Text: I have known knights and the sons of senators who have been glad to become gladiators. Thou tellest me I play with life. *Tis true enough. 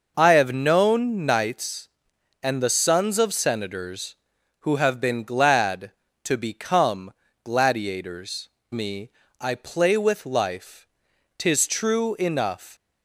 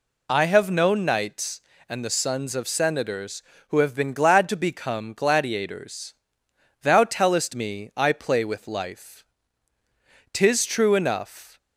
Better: second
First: pauses between "become" and "gladiators"; slight; at 7.1 s; 0.32 s long // skips "Thou tellest"; at 8.6 s // pauses between "me" and "I"; slight; at 9.0 s; 0.32 s long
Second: none

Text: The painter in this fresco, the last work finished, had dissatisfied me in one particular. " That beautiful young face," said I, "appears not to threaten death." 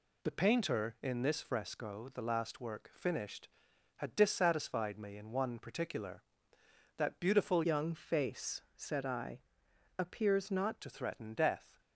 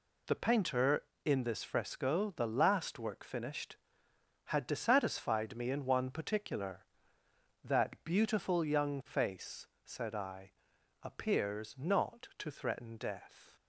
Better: second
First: changes voice from "young" to "not"; from 7.6 to 10.7 s; 3.1 s long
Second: none

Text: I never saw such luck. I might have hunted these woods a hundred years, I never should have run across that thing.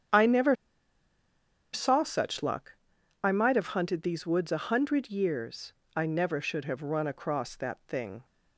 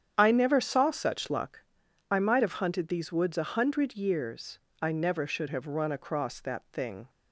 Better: second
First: starts louder than the rest; strong; until 2.3 s; 8.5 dB // pauses between "never" and "saw"; at 0.5 s; 1.1 s long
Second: starts louder than the rest; strong; until 1.1 s; 8.5 dB

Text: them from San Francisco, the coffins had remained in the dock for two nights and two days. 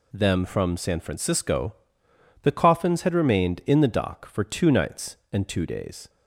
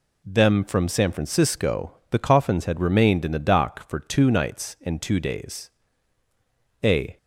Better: first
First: none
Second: goes on to say "A"; slight; from 6.8 s on; 0.34 s long

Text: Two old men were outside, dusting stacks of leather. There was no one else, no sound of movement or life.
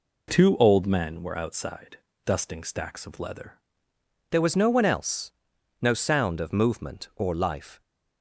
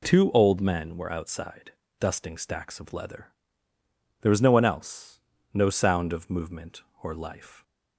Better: second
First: changes voice at "There"; from 4.3 s on; 3.5 s long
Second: none

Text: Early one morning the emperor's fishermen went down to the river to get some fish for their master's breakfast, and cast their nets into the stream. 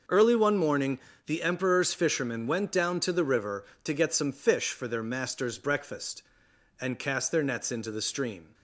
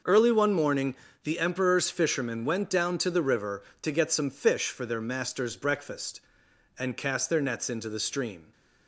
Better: neither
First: pauses between "morning" and "the"; slight; at 1.0 s; 0.24 s long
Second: pauses between "morning" and "the"; slight; at 0.9 s; 0.26 s long

